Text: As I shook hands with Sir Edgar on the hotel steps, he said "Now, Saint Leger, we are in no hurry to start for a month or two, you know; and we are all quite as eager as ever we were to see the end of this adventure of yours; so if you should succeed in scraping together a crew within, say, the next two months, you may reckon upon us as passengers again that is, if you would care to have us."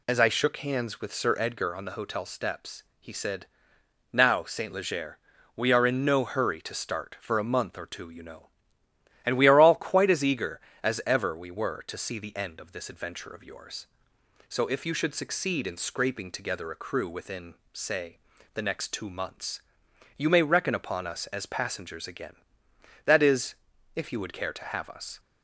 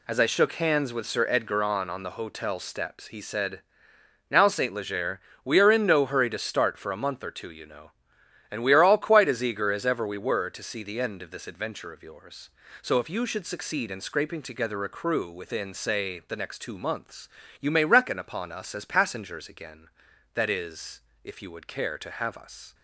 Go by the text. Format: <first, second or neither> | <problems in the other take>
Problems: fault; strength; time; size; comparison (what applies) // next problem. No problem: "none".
first | says "on" twice; at 1.8 s // pauses between "said" and "Now"; noticeable; at 3.5 s; 0.72 s long; noticeable in the first